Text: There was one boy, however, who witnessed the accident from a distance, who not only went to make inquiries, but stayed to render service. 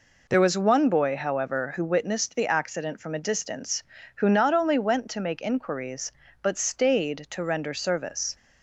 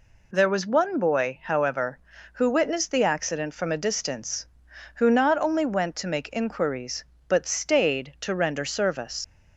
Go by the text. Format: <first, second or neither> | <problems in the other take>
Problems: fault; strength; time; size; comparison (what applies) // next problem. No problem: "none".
first | leaves "service" unfinished; at 9.2 s; 95 ms